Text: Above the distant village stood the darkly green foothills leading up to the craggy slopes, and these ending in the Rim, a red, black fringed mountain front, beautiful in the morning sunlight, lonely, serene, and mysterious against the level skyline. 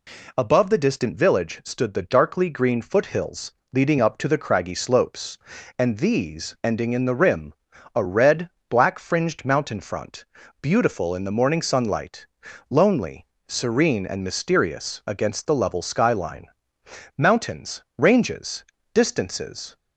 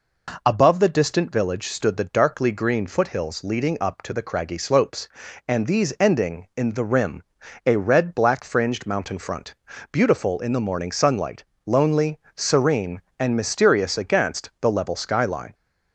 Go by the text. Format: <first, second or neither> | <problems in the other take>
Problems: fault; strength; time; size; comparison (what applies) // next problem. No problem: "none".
second | pauses between "foothills" and "leading"; slight; at 3.5 s; 0.22 s long // goes on to say "Mountains ranges distances"; strong; from 17.1 s on; 2.5 s long